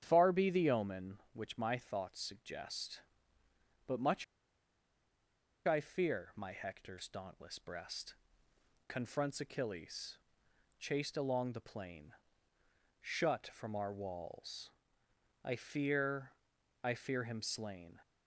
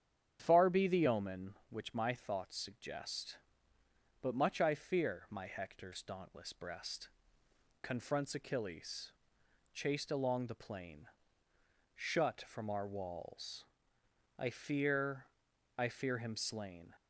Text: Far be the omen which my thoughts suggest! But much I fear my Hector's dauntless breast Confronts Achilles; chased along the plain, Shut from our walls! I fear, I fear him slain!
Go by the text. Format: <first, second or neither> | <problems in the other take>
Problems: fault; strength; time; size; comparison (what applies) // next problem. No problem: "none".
second | starts louder than the rest; strong; until 1.0 s; 9.5 dB; strong in the second // pauses between "much" and "I"; strong; at 4.2 s; 1.4 s long // pauses between "breast" and "Confronts"; noticeable; at 8.1 s; 0.74 s long; noticeable in the second